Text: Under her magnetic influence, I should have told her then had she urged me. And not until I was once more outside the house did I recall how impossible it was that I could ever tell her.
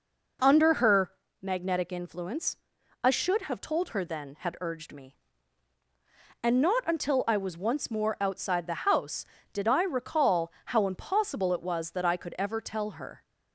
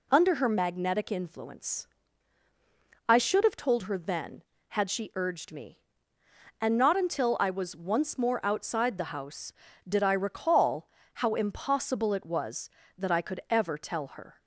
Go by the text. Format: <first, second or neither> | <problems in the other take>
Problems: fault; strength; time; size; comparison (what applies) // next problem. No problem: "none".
second | pauses between "her" and "magnetic"; slight; at 1.1 s; 0.32 s long // skips "she"; at 4.5 s // pauses between "recall" and "how"; slight; at 10.5 s; 0.16 s long; slight in the second